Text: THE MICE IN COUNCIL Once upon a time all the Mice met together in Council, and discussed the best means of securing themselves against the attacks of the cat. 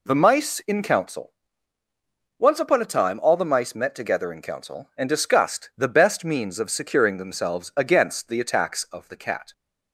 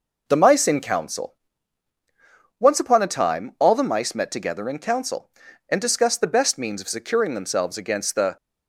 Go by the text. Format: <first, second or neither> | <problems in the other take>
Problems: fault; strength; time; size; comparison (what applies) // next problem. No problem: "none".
first | pauses between "COUNCIL" and "Once"; at 1.3 s; 1.2 s long; also in the first // stops before "attacks of the cat"; at 8.3 s